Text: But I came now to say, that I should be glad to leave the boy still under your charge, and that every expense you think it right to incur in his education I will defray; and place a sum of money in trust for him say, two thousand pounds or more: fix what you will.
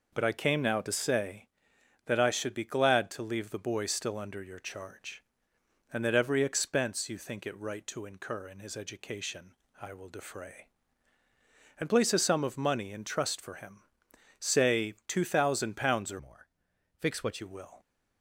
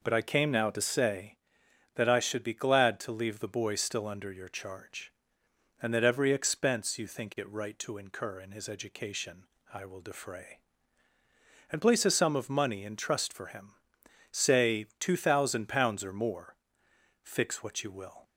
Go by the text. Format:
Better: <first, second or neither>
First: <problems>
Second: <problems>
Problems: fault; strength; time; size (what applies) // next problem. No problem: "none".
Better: second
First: pauses between "education" and "I"; slight; at 9.5 s; 0.28 s long // pauses between "him" and "say"; noticeable; at 13.7 s; 0.58 s long // changes voice from "more" to "what"; from 16.1 to 17.4 s; 1.3 s long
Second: pauses between "education" and "I"; slight; at 9.4 s; 0.28 s long // pauses between "him" and "say"; noticeable; at 13.7 s; 0.58 s long